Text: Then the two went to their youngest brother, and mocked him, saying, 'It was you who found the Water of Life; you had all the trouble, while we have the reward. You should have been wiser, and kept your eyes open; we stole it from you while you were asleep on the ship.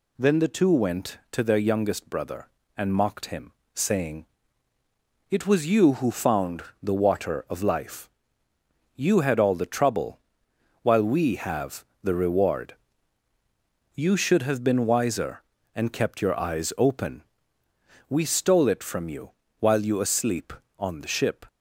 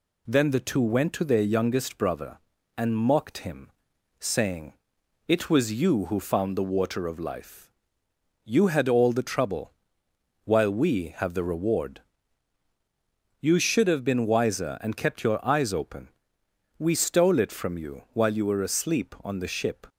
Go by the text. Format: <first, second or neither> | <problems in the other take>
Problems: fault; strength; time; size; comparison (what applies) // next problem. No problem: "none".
second | pauses between "found" and "the"; slight; at 6.6 s; 0.20 s long // pauses between "have" and "the"; slight; at 11.8 s; 0.18 s long // pauses between "you" and "while"; slight; at 19.3 s; 0.28 s long // skips "were"; at 19.9 s